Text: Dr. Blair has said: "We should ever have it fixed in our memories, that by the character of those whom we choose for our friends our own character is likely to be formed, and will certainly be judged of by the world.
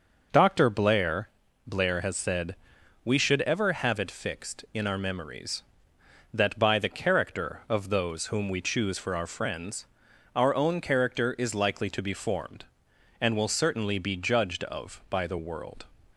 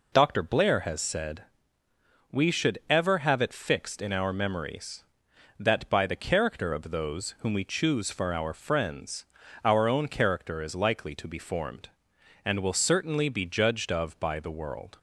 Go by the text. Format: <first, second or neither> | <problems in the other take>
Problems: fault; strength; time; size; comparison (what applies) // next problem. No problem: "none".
second | says "Blair" twice; at 1.6 s // pauses between "friends" and "our"; noticeable; at 9.8 s; 0.50 s long; also in the second